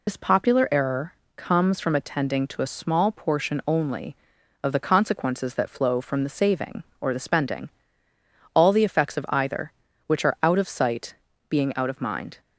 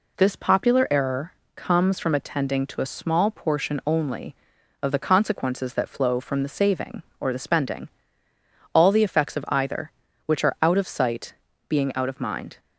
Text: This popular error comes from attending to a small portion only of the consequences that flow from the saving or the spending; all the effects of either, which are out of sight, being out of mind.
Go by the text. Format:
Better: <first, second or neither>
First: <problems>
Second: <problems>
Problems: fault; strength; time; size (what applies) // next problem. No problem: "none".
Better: second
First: loses the start of "This"; at 0.0 s; 95 ms // pauses between "error" and "comes"; slight; at 1.1 s; 0.24 s long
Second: pauses between "error" and "comes"; slight; at 1.3 s; 0.24 s long